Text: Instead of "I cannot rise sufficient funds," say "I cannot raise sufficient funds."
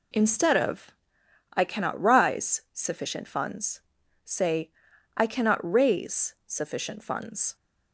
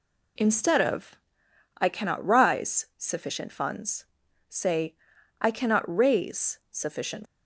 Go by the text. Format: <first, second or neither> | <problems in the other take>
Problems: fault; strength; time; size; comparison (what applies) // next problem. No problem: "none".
first | pauses between "of" and "I"; noticeable; at 1.1 s; 0.62 s long; noticeable in the first // pauses between "say" and "I"; noticeable; at 4.9 s; 0.46 s long; noticeable in the first // stops before "funds"; at 7.2 s